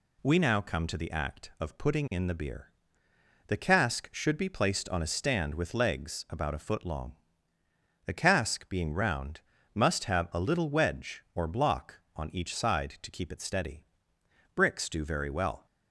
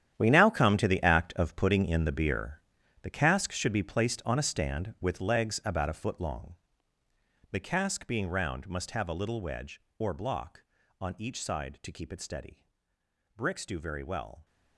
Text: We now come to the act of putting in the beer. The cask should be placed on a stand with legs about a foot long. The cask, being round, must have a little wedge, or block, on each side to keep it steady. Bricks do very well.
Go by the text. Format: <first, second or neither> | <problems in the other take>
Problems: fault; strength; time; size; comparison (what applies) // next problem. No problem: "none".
first | gets quieter; strong; throughout; 13.5 dB